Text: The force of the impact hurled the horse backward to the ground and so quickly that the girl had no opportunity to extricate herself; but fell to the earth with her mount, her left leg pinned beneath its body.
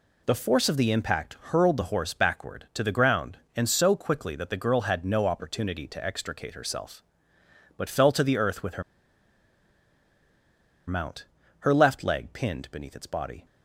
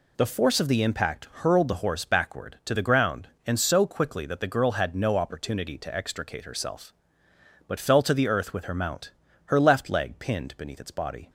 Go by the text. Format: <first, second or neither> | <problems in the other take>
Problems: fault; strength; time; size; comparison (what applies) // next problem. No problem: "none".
second | pauses between "her" and "mount"; strong; at 8.8 s; 2.0 s long